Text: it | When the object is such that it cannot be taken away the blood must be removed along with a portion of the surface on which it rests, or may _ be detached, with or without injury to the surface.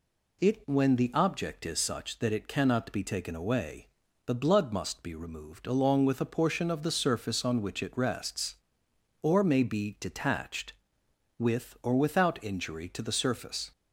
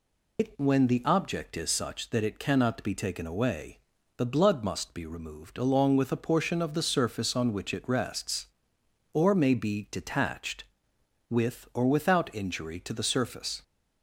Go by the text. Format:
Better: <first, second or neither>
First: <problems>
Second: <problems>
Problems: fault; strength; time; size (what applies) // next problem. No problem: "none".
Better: first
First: pauses between "away" and "the"; at 3.8 s; 0.40 s long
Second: loses the start of "it"; at 0.3 s; 90 ms // pauses between "away" and "the"; at 3.7 s; 0.40 s long